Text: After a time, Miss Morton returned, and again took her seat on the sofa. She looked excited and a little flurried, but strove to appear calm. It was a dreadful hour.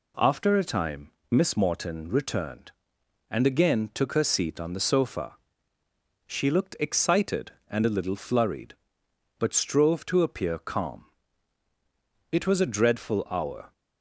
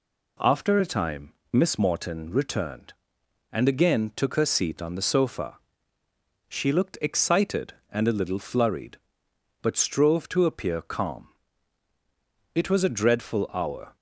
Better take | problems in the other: neither | none

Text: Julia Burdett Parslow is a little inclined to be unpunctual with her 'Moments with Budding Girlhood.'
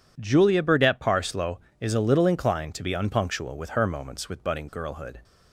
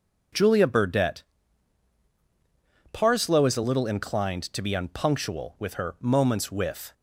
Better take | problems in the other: first | pauses between "Burdett" and "Parslow"; strong; at 1.2 s; 1.7 s long // stops before "Budding Girlhood"; at 6.9 s

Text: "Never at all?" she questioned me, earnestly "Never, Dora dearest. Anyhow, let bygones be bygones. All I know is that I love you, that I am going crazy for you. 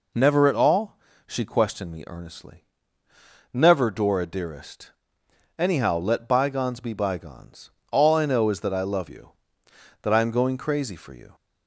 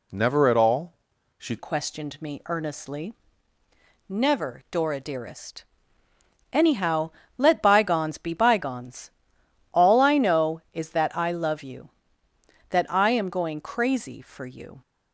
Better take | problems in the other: first | changes voice at "questioned"; from 1.5 s on; 13.3 s long // pauses between "earnestly" and "Never"; noticeable; at 3.1 s; 0.96 s long; noticeable in the first

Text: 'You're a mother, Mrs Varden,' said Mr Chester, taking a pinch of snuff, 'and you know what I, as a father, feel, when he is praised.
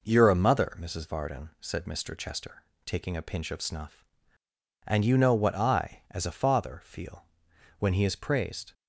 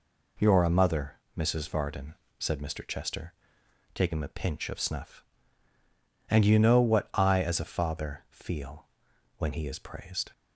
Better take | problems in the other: neither | none

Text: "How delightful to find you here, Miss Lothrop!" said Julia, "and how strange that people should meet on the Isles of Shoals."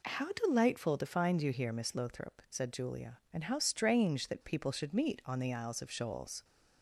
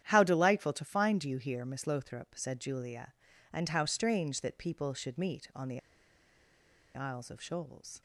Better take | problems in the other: first | starts louder than the rest; strong; until 1.0 s; 10.5 dB // pauses between "the" and "Isles"; at 5.7 s; 1.1 s long

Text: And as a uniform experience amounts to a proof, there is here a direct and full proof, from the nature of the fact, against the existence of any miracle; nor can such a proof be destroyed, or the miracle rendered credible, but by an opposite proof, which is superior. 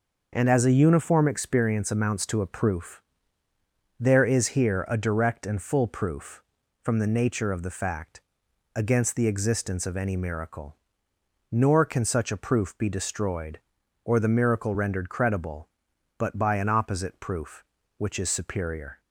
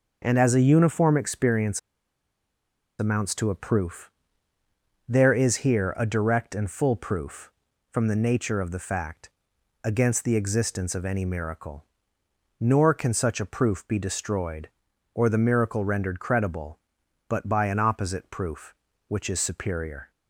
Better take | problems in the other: first | pauses between "experience" and "amounts"; at 1.7 s; 1.2 s long

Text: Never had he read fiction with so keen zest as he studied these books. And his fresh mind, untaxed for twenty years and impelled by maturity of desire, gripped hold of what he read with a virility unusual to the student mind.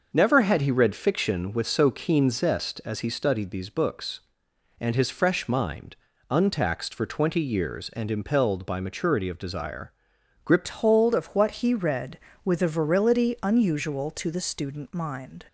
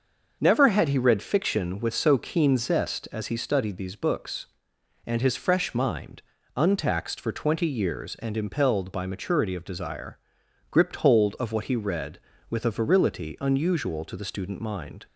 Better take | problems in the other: second | starts louder than the rest; noticeable; until 1.1 s; 6 dB; noticeable in the second // changes voice at "hold"; from 10.6 s on; 4.8 s long

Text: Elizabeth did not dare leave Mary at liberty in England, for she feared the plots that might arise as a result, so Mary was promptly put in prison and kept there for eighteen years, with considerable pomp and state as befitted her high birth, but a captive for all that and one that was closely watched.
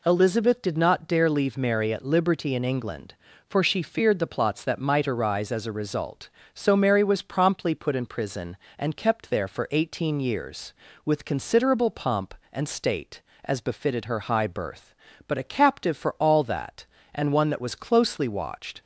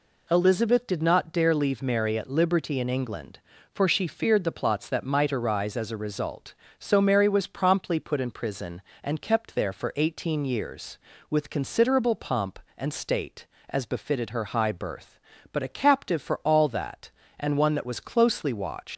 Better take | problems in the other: first | leaves "watched" unfinished; at 18.9 s; 100 ms

